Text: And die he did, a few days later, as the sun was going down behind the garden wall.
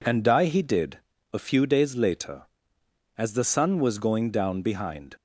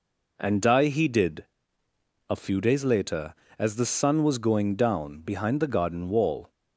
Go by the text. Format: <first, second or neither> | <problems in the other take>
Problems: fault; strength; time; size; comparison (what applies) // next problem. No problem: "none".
second | stops before "the garden wall"; at 5.1 s